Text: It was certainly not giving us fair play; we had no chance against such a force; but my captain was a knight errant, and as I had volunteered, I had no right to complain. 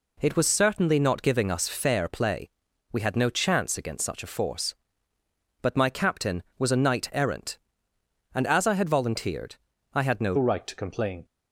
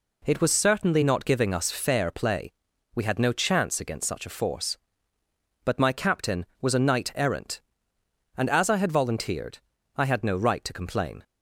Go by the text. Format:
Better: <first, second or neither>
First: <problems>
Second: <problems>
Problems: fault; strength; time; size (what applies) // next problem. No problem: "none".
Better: second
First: changes voice at "right"; from 10.3 s on; 0.9 s long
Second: none